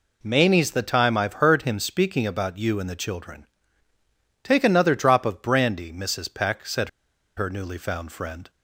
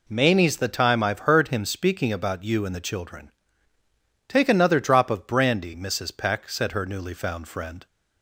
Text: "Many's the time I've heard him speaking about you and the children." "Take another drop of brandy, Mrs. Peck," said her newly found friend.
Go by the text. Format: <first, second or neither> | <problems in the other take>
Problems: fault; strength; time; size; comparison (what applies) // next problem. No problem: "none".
second | pauses between "said" and "her"; noticeable; at 6.8 s; 0.48 s long